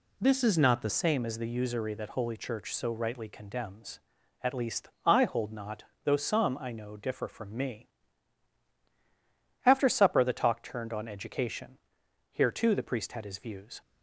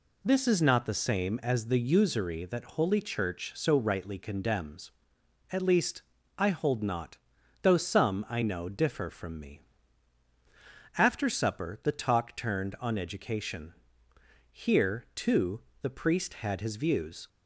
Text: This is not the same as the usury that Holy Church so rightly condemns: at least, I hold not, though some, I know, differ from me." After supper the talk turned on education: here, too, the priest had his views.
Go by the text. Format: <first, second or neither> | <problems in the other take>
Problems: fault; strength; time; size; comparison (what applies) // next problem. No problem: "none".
second | changes voice at "same"; from 0.8 s on; 13.0 s long